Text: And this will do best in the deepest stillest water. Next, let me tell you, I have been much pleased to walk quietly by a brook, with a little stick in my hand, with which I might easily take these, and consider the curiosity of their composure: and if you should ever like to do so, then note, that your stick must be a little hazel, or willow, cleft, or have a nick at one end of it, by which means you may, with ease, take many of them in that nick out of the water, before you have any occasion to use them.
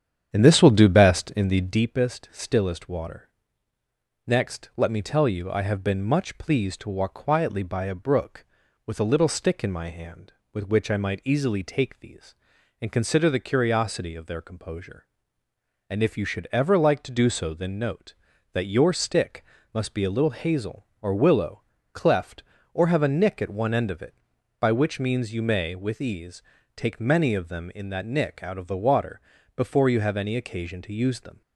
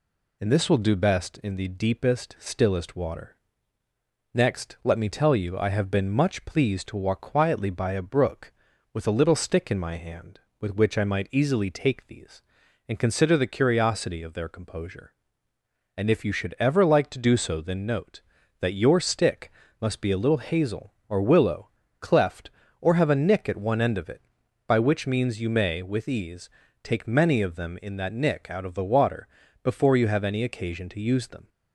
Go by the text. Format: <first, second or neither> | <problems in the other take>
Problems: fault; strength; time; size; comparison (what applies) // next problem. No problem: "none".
second | starts louder than the rest; strong; until 1.8 s; 8.5 dB // pauses between "stick" and "must"; slight; at 19.4 s; 0.32 s long; slight in the second